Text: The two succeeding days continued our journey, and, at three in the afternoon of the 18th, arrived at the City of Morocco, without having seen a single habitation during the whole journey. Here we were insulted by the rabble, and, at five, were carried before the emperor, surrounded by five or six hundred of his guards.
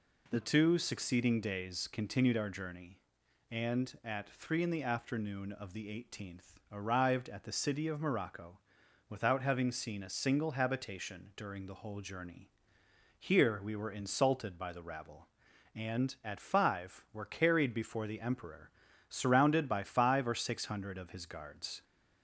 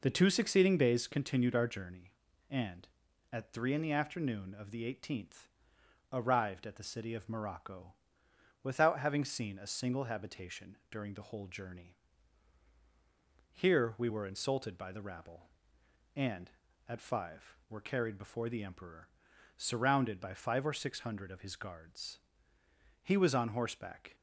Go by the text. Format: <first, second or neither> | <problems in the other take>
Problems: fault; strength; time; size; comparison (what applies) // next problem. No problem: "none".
first | goes on to say "He was on horseback"; noticeable; from 23.0 s on; 1.1 s long